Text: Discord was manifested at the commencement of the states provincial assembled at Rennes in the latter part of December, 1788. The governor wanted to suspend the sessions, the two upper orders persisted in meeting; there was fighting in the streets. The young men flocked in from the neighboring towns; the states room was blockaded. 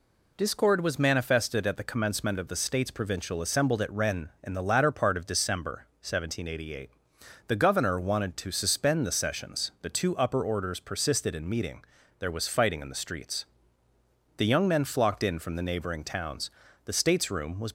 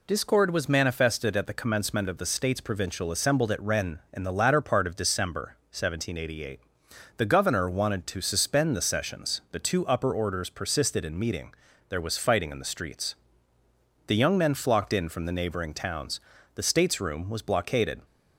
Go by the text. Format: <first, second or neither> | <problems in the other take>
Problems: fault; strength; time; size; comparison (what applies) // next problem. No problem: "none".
second | stops before "blockaded"; at 17.6 s